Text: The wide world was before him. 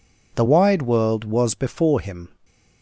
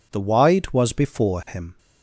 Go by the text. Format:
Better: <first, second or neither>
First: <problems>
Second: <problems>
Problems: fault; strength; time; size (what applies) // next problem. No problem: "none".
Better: first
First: none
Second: skips "world"; at 0.7 s